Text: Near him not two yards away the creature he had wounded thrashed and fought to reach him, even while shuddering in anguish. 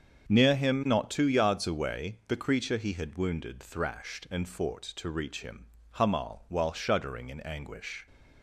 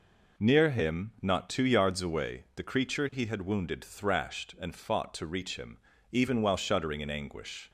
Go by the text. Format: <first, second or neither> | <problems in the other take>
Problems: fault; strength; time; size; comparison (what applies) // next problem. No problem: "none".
second | starts louder than the rest; until 1.3 s; 7 dB // says "hamal" for "even"; at 5.9 s